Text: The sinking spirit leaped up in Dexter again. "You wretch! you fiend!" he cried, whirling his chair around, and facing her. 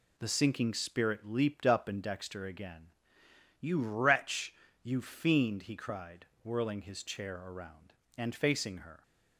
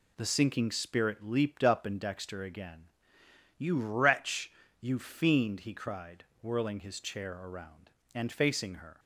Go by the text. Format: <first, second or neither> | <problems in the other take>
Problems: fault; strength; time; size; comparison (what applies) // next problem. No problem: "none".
neither | none